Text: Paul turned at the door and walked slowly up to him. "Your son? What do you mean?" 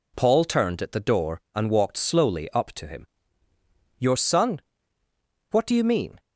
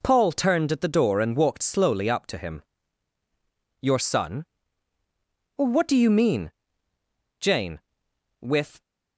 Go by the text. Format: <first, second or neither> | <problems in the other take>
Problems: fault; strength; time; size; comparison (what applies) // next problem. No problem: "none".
first | goes on to say "Jane with"; from 7.3 s on; 1.4 s long